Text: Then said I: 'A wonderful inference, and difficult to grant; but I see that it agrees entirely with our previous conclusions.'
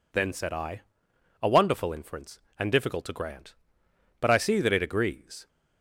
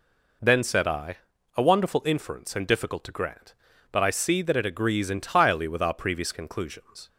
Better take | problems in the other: second | stops before "entirely with our previous conclusions"; at 5.4 s

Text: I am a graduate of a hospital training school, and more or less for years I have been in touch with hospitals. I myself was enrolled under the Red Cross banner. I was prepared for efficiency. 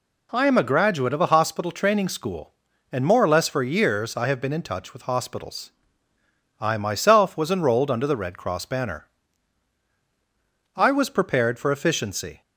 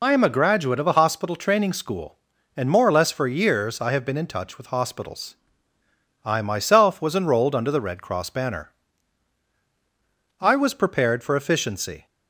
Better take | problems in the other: first | loses the start of "I"; at 0.0 s; 45 ms

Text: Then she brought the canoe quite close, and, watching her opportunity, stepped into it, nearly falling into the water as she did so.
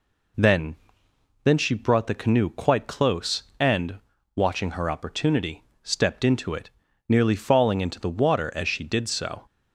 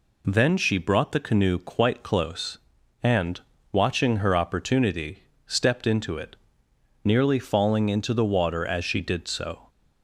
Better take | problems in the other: second | says "Then" twice; at 1.4 s

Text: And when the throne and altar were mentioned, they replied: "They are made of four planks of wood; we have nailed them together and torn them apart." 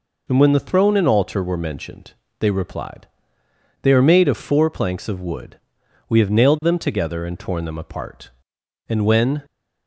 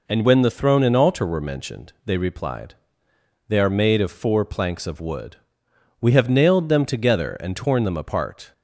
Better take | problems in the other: second | goes on to say "And when"; from 8.8 s on; 0.56 s long

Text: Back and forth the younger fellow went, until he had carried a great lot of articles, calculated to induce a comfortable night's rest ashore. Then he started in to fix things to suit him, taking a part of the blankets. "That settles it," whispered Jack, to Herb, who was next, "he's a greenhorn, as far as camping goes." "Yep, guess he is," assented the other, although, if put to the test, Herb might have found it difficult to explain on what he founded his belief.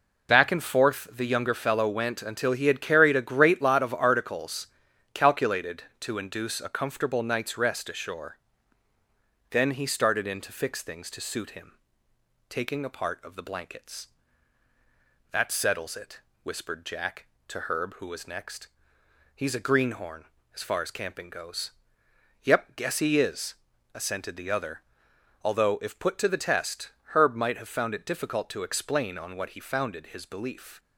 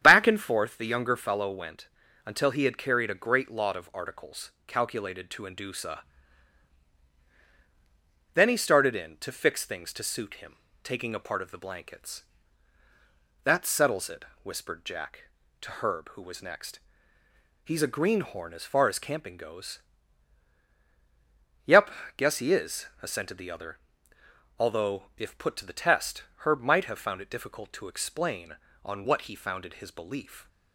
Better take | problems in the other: first | starts louder than the rest; strong; until 1.0 s; 9.5 dB // skips "comfortable night's rest ashore"; at 7.1 s

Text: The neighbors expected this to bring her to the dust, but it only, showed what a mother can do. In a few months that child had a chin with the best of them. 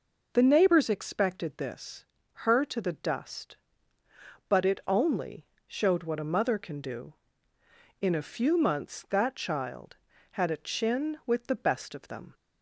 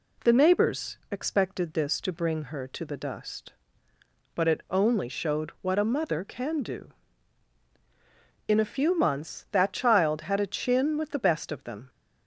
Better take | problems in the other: second | skips "to bring"; at 2.2 s

